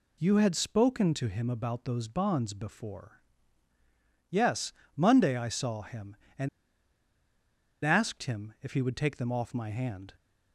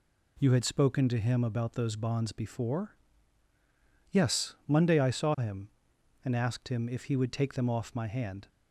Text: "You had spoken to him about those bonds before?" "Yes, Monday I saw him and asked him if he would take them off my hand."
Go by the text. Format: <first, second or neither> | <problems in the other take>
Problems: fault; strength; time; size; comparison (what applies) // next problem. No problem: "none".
second | pauses between "and" and "asked"; strong; at 6.4 s; 1.3 s long